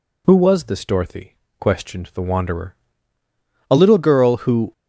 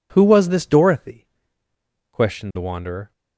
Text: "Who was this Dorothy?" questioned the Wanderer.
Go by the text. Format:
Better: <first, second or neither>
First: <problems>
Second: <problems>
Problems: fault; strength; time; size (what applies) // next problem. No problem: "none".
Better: second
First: goes on to say "A little girl who"; noticeable; from 3.6 s on; 1.0 s long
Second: none